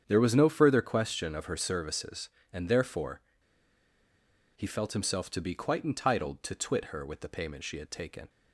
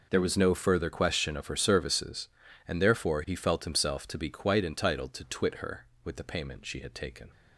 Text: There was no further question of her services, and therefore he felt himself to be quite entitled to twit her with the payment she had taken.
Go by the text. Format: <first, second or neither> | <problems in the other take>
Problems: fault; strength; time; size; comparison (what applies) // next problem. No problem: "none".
second | starts louder than the rest; strong; until 1.0 s; 8.5 dB // pauses between "therefore" and "he"; strong; at 3.2 s; 1.3 s long